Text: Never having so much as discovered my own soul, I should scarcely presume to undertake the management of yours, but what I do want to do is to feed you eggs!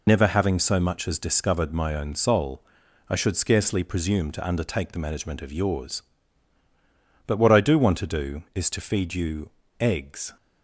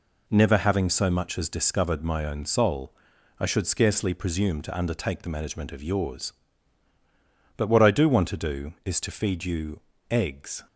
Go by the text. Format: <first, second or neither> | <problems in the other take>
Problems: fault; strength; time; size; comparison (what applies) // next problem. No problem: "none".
second | loses the start of "Never"; at 0.0 s; 90 ms // pauses between "you" and "eggs"; slight; at 9.4 s; 0.32 s long; slight in the second